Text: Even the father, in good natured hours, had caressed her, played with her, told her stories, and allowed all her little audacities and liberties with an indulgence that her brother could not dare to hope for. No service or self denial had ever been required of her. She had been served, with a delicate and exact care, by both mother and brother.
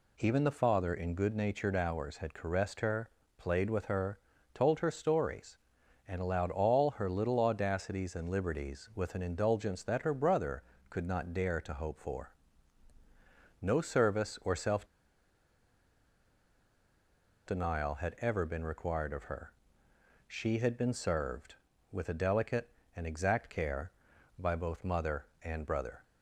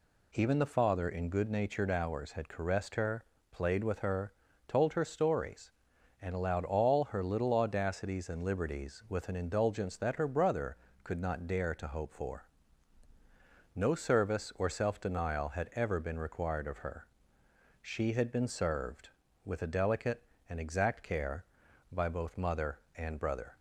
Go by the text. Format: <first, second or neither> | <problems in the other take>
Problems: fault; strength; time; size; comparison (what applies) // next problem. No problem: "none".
second | pauses between "self" and "denial"; strong; at 14.8 s; 2.6 s long